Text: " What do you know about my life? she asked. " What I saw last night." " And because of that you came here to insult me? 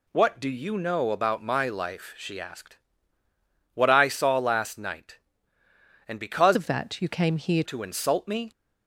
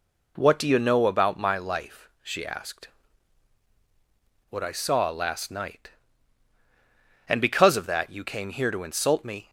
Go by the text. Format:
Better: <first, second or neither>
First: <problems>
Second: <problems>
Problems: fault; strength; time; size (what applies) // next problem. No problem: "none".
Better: second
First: changes voice from "of" to "here"; from 6.5 to 7.6 s; 1.1 s long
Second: none